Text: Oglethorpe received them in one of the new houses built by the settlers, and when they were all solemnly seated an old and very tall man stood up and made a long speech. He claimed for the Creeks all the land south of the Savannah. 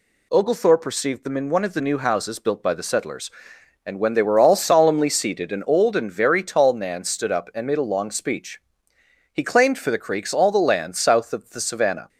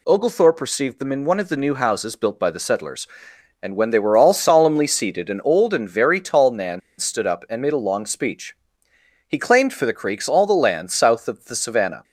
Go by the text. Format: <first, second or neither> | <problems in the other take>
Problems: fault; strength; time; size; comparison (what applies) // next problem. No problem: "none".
first | pauses between "man" and "stood"; slight; at 6.8 s; 0.18 s long